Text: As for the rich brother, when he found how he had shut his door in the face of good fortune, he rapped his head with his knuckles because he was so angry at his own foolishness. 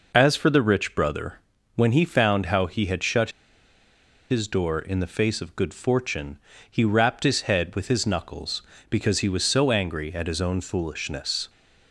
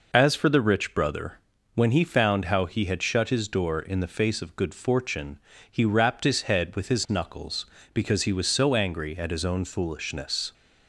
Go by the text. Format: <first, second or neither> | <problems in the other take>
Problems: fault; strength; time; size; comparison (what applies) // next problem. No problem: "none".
second | pauses between "shut" and "his"; at 3.2 s; 1.0 s long